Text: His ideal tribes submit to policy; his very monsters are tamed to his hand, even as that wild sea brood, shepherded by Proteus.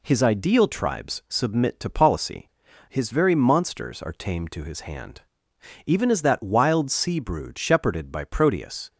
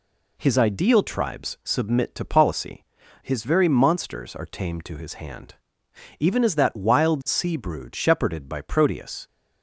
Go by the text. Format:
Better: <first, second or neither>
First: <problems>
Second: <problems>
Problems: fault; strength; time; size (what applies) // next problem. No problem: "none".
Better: neither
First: none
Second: none